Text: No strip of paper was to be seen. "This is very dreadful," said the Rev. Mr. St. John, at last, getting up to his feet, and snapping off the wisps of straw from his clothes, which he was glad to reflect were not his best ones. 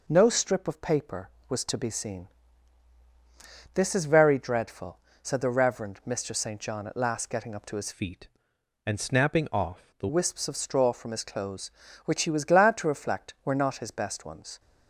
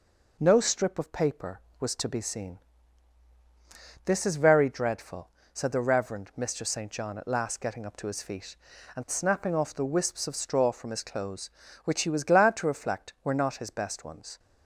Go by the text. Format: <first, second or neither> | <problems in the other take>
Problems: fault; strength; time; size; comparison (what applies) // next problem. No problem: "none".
second | changes voice from "feet" to "the"; from 7.9 to 10.0 s; 2.1 s long